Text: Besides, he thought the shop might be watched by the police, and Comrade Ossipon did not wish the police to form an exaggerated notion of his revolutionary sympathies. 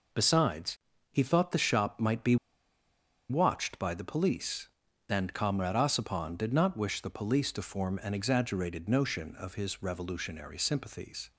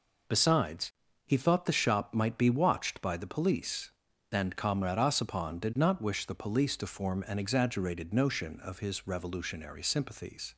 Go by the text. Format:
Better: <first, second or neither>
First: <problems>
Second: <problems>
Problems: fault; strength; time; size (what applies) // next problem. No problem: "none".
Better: second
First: pauses between "be" and "watched"; noticeable; at 2.3 s; 0.94 s long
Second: none